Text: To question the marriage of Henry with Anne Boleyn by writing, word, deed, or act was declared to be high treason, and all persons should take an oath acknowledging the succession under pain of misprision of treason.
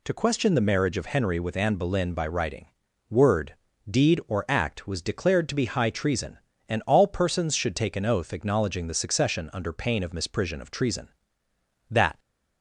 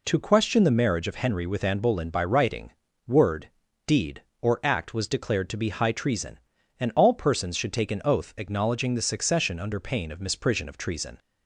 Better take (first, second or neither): second